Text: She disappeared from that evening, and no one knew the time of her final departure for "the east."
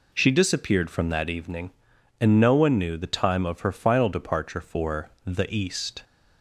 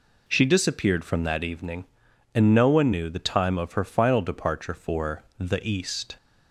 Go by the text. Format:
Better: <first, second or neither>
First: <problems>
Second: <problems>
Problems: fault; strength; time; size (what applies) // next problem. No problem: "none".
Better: neither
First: none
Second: none